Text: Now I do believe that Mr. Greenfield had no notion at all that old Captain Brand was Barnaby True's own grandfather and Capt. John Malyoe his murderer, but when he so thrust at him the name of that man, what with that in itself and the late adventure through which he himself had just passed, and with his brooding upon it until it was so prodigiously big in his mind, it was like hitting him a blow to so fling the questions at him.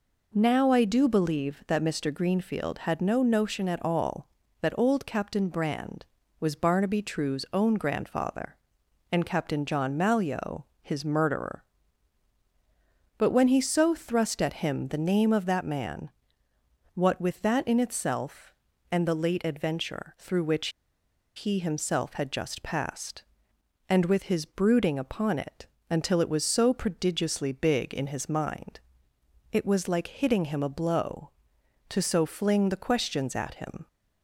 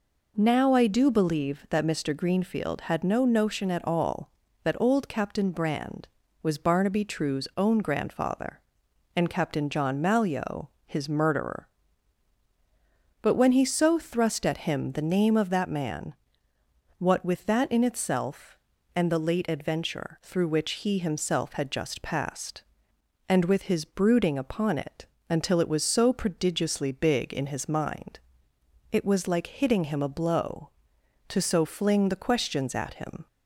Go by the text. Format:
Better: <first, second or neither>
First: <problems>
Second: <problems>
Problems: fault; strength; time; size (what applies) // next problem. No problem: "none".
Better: second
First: pauses between "Malyoe" and "his"; slight; at 10.6 s; 0.18 s long // pauses between "which" and "he"; noticeable; at 20.6 s; 0.67 s long // pauses between "it" and "until"; slight; at 25.6 s; 0.24 s long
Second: pauses between "Malyoe" and "his"; slight; at 10.6 s; 0.18 s long // pauses between "it" and "until"; slight; at 25.0 s; 0.24 s long